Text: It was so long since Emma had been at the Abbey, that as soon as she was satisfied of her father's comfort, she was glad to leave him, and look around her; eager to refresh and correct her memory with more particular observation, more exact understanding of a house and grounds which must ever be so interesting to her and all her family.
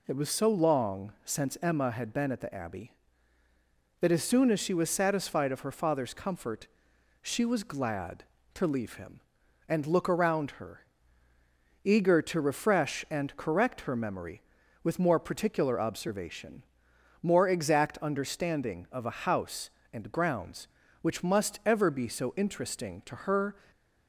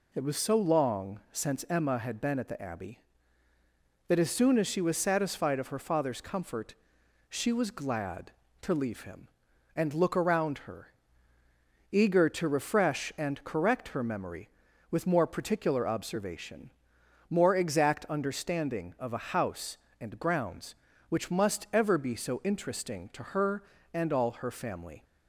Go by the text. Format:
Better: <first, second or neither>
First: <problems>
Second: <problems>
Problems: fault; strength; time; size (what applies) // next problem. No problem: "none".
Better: second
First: stops before "and all her family"; at 23.7 s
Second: none